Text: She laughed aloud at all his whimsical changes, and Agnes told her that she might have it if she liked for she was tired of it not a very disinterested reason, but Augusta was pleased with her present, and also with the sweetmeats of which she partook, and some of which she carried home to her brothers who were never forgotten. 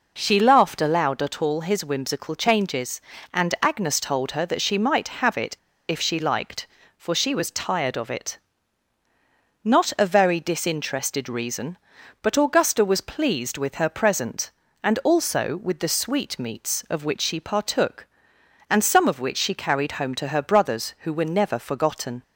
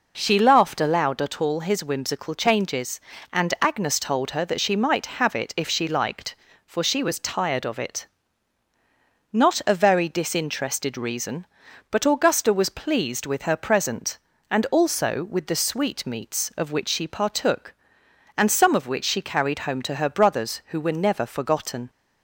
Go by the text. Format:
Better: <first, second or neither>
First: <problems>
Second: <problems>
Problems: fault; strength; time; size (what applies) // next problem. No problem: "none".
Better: second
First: pauses between "it" and "if"; slight; at 5.5 s; 0.33 s long // pauses between "it" and "not"; at 8.3 s; 1.2 s long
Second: pauses between "it" and "not"; at 8.0 s; 1.2 s long